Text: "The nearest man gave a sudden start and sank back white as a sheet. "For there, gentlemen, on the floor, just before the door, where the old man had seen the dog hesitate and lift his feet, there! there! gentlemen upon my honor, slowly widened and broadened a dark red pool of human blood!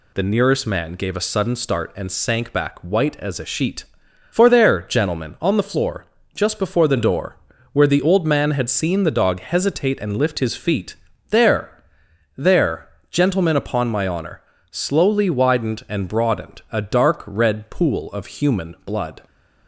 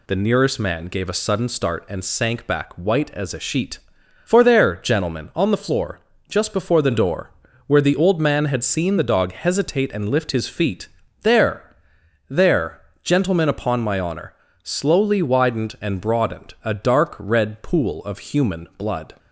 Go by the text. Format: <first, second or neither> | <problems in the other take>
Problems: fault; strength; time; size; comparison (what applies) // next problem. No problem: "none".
neither | none